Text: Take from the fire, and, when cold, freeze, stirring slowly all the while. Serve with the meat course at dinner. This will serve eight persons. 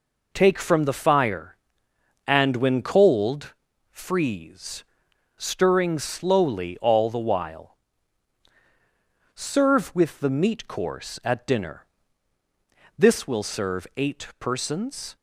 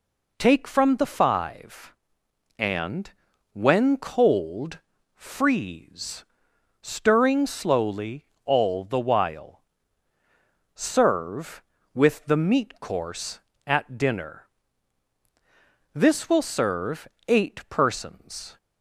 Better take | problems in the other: first | says "five" for "fire"; at 1.0 s // pauses between "slowly" and "all"; slight; at 8.2 s; 0.20 s long // pauses between "serve" and "eight"; slight; at 17.0 s; 0.22 s long

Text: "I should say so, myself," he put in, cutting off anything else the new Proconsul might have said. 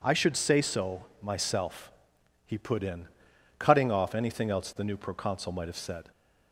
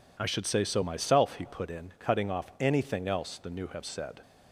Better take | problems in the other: first | skips "Proconsul might"; at 3.6 s

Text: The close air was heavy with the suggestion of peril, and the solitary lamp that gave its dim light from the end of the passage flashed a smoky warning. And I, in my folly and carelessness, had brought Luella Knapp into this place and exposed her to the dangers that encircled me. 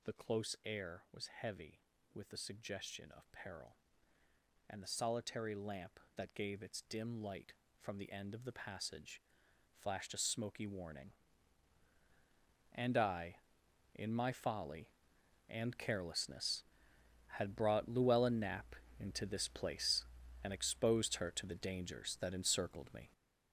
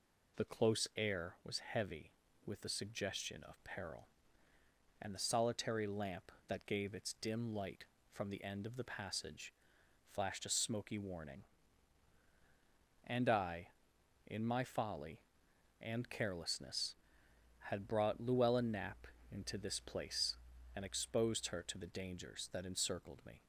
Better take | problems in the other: second | gets louder; strong; throughout; 7.5 dB // pauses between "passage" and "flashed"; noticeable; at 9.2 s; 0.58 s long; noticeable in the second // pauses between "Knapp" and "into"; slight; at 18.7 s; 0.24 s long; slight in the second

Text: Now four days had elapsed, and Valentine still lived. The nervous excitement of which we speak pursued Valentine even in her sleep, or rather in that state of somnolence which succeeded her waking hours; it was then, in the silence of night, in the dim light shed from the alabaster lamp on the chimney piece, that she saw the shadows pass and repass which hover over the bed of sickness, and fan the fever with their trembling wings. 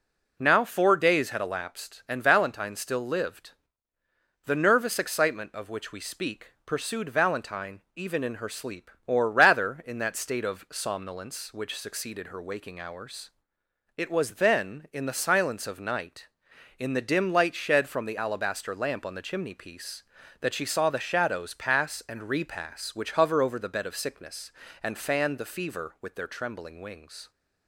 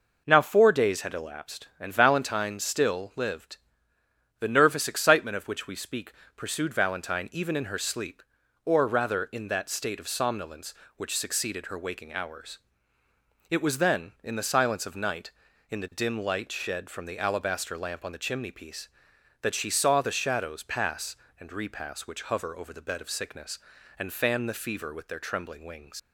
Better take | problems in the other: first | pauses between "speak" and "pursued"; slight; at 6.1 s; 0.24 s long // leaves "wings" unfinished; at 25.9 s; 70 ms

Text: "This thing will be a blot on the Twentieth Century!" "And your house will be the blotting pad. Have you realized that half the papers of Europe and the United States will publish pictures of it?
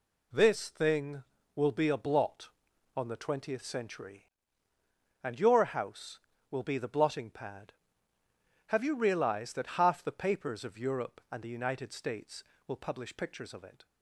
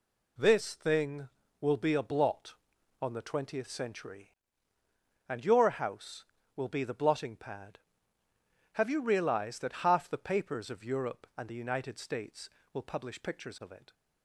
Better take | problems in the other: neither | none

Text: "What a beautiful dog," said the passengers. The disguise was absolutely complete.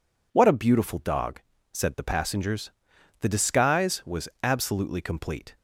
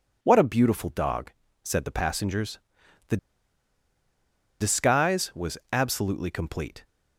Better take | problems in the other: first | pauses between "The" and "disguise"; strong; at 3.1 s; 1.4 s long

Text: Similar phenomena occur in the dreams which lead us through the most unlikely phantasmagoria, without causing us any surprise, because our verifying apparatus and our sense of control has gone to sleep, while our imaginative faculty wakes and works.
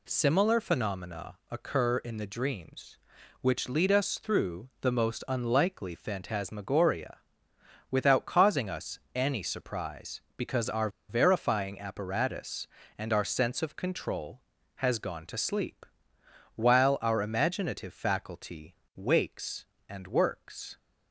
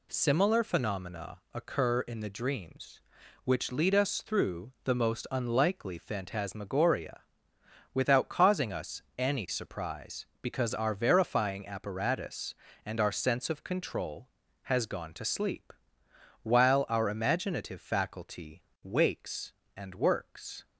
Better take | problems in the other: second | pauses between "phenomena" and "occur"; slight; at 1.3 s; 0.16 s long; slight in the second // pauses between "us" and "any"; slight; at 8.9 s; 0.18 s long; slight in the second // pauses between "our" and "verifying"; slight; at 10.8 s; 0.20 s long // pauses between "faculty" and "wakes"; slight; at 18.7 s; 0.22 s long; slight in the second

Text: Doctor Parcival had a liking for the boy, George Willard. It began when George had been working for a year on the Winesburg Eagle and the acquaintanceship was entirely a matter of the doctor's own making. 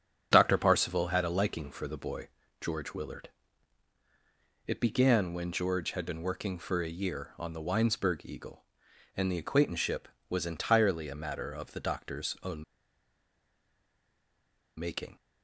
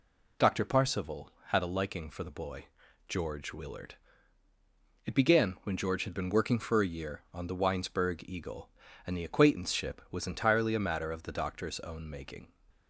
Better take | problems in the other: second | starts louder than the rest; strong; until 1.3 s; 7.5 dB // pauses between "own" and "making"; strong; at 12.6 s; 2.1 s long

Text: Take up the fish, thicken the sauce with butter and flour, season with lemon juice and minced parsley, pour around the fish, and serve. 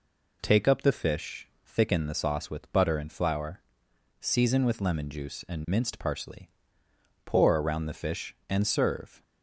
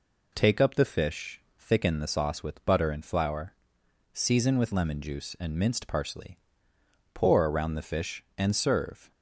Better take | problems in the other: neither | none

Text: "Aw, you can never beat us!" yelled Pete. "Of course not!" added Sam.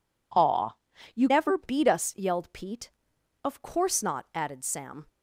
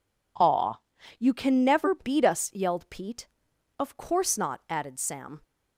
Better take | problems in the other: second | skips "can"; at 1.2 s

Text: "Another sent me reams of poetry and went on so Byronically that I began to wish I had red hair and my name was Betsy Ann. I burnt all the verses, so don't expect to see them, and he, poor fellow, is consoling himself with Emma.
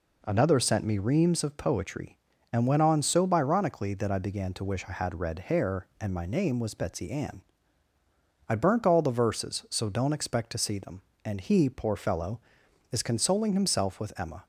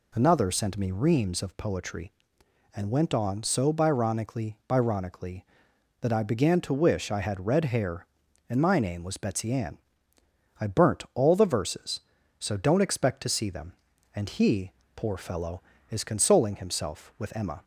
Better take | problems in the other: first | says "Byronically" twice; at 4.6 s

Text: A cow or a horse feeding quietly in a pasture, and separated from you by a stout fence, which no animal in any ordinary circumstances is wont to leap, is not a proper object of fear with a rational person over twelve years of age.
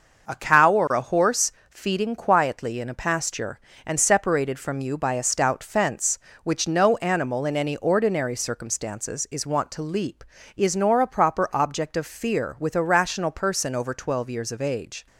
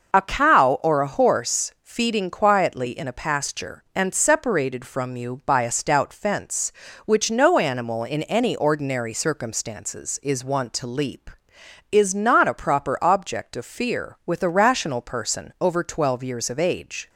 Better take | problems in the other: second | starts louder than the rest; until 1.3 s; 6 dB // pauses between "horse" and "feeding"; slight; at 1.5 s; 0.18 s long // says "nor" for "not"; at 10.7 s

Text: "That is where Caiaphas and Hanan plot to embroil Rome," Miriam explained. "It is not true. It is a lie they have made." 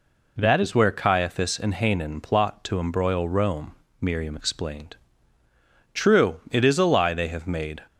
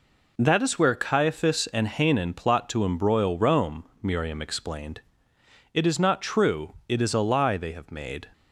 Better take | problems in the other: second | skips "It is not"; at 5.4 s

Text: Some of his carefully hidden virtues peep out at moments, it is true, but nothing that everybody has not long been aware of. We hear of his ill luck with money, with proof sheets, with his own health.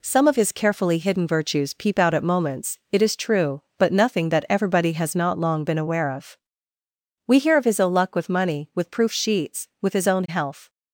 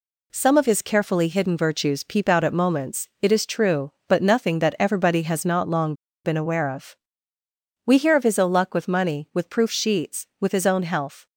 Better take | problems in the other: first | pauses between "long" and "been"; slight; at 5.9 s; 0.31 s long

